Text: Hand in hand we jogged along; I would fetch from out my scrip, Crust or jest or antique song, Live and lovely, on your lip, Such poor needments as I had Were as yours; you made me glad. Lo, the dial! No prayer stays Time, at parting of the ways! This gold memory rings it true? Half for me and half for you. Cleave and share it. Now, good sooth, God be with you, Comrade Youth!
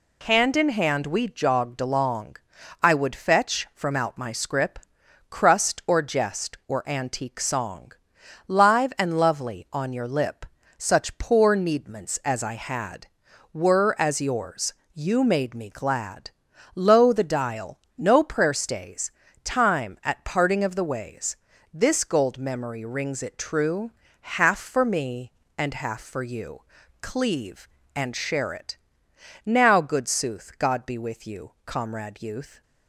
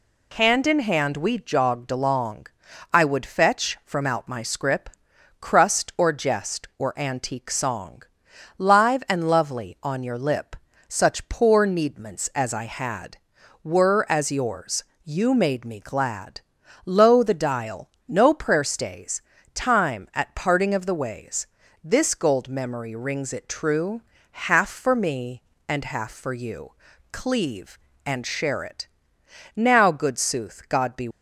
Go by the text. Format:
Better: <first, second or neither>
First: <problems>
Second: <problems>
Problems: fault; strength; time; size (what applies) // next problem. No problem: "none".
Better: first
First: pauses between "stays" and "Time"; slight; at 19.0 s; 0.32 s long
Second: pauses between "stays" and "Time"; slight; at 19.2 s; 0.32 s long // stops before "with you Comrade Youth"; at 31.1 s